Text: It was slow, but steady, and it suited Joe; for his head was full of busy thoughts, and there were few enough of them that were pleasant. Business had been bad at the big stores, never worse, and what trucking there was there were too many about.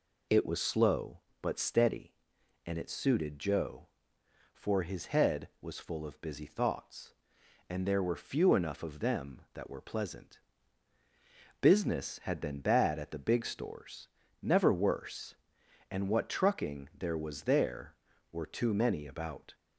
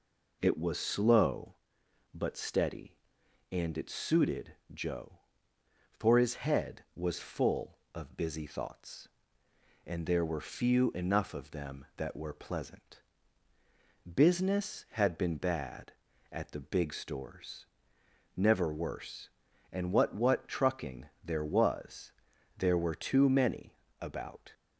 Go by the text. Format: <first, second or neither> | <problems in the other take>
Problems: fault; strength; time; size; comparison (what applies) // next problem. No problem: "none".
first | pauses between "suited" and "Joe"; slight; at 4.5 s; 0.18 s long // says "what" twice; at 20.1 s // pauses between "was" and "there"; noticeable; at 22.1 s; 0.46 s long // pauses between "many" and "about"; slight; at 23.7 s; 0.24 s long